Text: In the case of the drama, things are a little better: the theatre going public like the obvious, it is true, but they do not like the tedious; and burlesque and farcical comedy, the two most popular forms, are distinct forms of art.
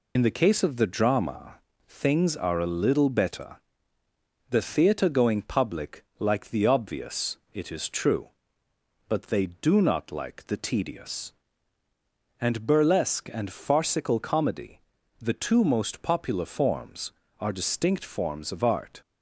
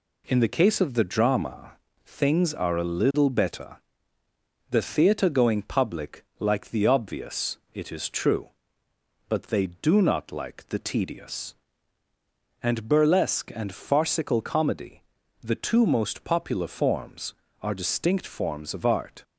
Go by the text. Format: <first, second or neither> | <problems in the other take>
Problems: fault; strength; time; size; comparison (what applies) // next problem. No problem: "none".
second | loses the start of "In"; at 0.1 s; 65 ms // pauses between "public" and "like"; slight; at 6.0 s; 0.16 s long; slight in the second